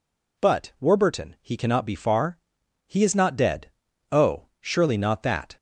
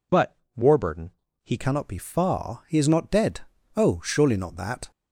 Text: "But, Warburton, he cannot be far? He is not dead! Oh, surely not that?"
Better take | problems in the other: first | changes voice at "cannot"; from 1.5 s on; 3.4 s long

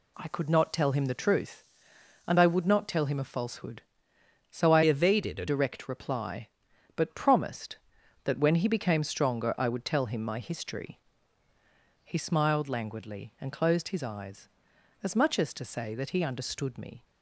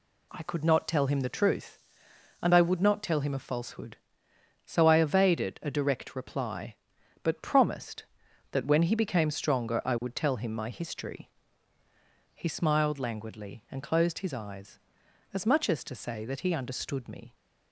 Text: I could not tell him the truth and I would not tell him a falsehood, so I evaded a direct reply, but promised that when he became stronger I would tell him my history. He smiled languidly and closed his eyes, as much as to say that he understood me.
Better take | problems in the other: second | changes voice from "evaded" to "a"; from 4.8 to 5.4 s; 0.6 s long

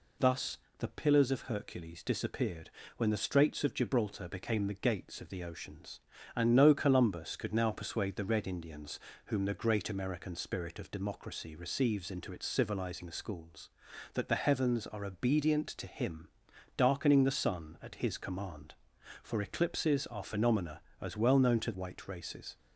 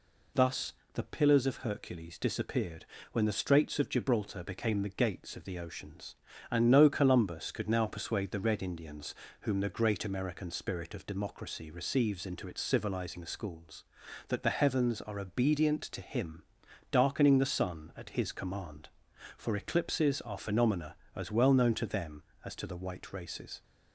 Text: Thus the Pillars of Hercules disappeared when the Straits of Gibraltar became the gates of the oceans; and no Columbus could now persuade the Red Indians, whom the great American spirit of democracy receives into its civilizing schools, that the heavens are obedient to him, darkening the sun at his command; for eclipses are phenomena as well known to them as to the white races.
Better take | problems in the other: second | pauses between "Thus" and "the"; slight; at 0.5 s; 0.20 s long; slight in the second // pauses between "disappeared" and "when"; slight; at 2.7 s; 0.26 s long; slight in the second // skips "them as to the"; at 21.7 s

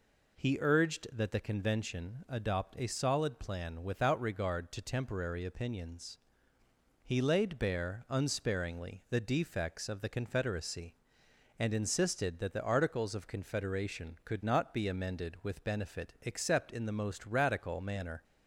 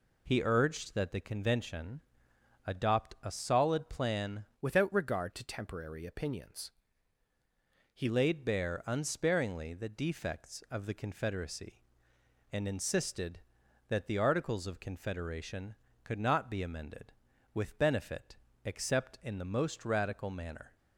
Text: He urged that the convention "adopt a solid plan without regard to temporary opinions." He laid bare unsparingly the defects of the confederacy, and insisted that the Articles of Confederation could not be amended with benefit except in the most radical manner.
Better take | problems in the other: first | pauses between "convention" and "adopt"; noticeable; at 2.0 s; 0.64 s long // changes voice from "without" to "He"; from 4.6 to 8.0 s; 3.4 s long // pauses between "benefit" and "except"; slight; at 18.3 s; 0.28 s long

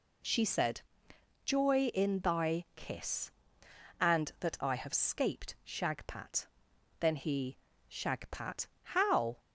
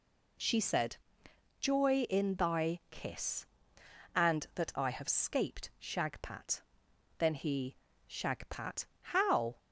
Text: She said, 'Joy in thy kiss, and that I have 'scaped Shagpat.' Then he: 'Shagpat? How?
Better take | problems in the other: neither | none

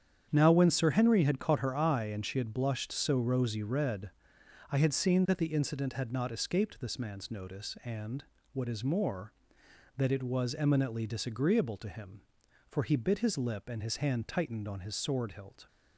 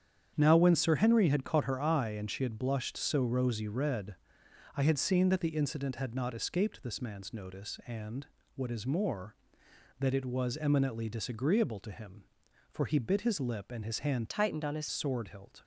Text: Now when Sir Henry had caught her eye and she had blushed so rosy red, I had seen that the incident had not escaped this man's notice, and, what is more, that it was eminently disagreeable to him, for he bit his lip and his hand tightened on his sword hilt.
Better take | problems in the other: first | starts louder than the rest; strong; until 1.3 s; 8.5 dB; strong in the first // changes voice from "tightened" to "his"; from 14.2 to 14.8 s; 0.6 s long

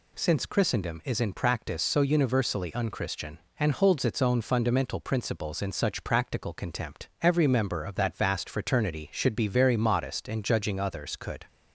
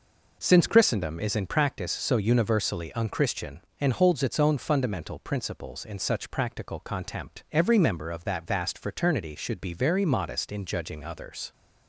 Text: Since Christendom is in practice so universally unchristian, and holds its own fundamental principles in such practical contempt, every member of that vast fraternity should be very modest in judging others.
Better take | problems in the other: second | goes on to say "Could"; slight; from 11.1 s on; 0.30 s long

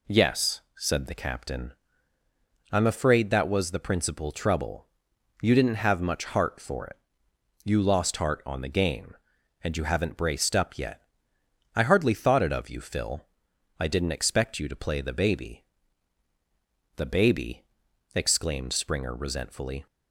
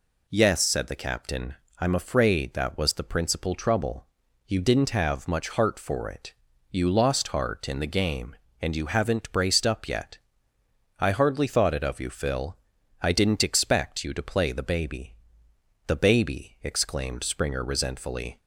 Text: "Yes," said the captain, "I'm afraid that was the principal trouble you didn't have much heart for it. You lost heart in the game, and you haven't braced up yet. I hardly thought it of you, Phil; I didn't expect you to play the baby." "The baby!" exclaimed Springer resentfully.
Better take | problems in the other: second | pauses between "trouble" and "you"; noticeable; at 4.8 s; 0.52 s long; also in the second // says "on" for "in"; at 8.4 s

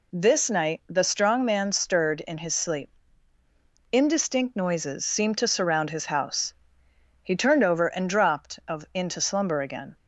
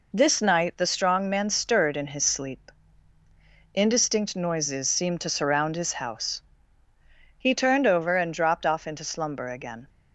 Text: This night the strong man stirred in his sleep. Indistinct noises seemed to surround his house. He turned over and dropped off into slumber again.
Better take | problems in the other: second | says "of" for "off"; at 8.6 s

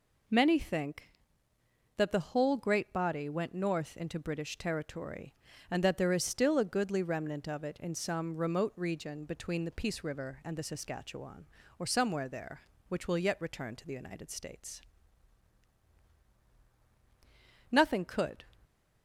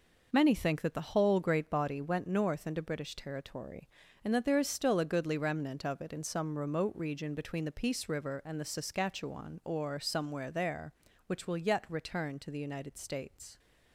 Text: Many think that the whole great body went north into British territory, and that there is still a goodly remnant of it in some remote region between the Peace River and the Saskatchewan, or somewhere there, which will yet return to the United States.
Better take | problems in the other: second | goes on to say "Nothing could"; noticeable; from 17.7 s on; 0.76 s long

